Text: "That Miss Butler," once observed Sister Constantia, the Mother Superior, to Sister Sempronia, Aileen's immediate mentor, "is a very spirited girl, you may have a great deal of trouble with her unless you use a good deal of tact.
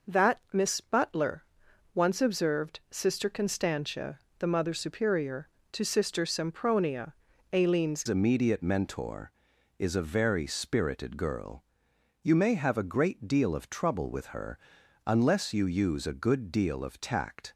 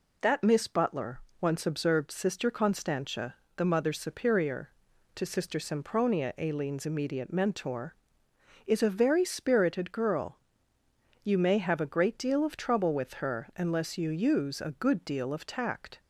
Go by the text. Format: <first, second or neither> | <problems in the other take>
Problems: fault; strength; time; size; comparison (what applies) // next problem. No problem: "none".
second | changes voice at "immediate"; from 8.0 s on; 9.5 s long // pauses between "her" and "unless"; noticeable; at 14.5 s; 0.48 s long